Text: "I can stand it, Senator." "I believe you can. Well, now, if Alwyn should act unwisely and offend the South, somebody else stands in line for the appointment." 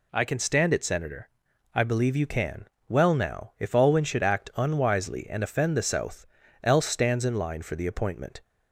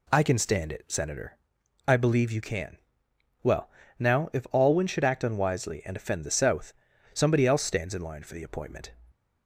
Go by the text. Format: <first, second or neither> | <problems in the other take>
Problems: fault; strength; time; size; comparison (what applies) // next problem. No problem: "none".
second | skips "somebody"; at 6.4 s